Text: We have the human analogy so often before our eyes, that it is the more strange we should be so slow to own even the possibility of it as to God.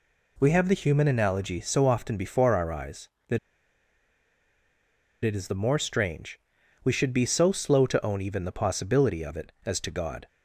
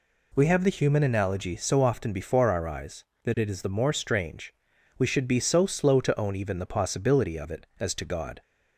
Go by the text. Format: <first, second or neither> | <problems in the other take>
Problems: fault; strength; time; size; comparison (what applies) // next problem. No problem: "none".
second | pauses between "that" and "it"; strong; at 3.3 s; 1.8 s long // pauses between "strange" and "we"; at 6.3 s; 0.44 s long; also in the second